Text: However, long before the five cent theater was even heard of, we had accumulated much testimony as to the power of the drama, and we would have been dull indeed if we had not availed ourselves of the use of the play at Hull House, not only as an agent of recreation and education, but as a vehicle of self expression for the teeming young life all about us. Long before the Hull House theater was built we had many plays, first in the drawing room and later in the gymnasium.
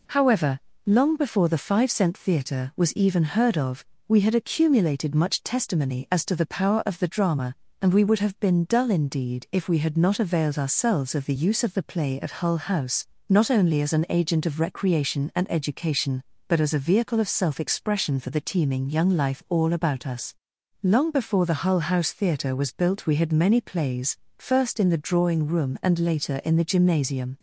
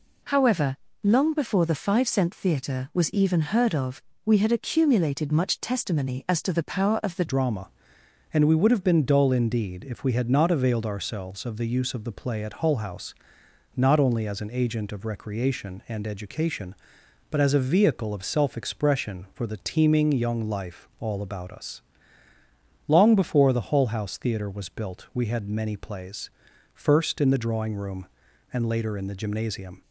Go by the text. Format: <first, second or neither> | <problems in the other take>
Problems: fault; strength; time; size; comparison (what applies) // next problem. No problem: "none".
first | changes voice at "drama"; from 7.2 s on; 22.6 s long